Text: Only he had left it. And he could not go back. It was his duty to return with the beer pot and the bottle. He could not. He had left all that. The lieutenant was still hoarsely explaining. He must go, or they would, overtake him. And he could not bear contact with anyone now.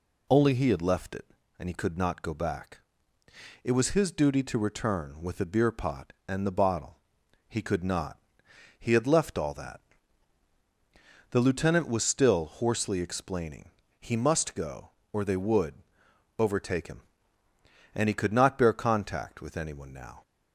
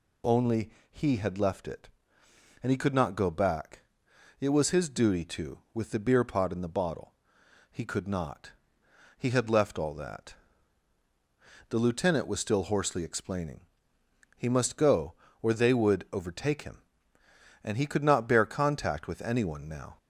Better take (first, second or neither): first